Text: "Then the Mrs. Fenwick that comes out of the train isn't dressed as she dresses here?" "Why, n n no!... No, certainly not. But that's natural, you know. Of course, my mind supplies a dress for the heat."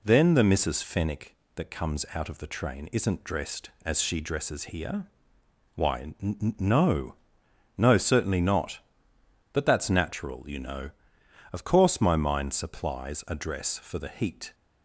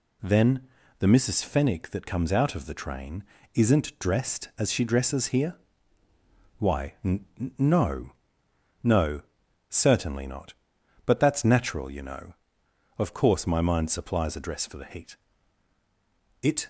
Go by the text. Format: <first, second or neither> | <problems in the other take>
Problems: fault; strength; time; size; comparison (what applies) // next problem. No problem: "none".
first | pauses between "Then" and "the"; slight; at 0.6 s; 0.32 s long // pauses between "train" and "isn't"; slight; at 3.2 s; 0.30 s long // goes on to say "It"; slight; from 16.4 s on; 0.26 s long